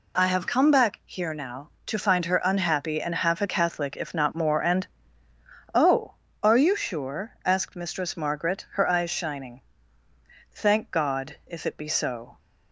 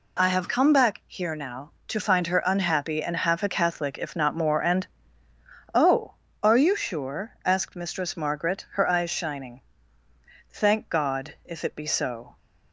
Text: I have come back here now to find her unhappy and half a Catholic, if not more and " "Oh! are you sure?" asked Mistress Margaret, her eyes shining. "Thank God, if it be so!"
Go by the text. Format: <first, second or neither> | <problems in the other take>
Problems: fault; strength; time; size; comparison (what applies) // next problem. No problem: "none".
neither | none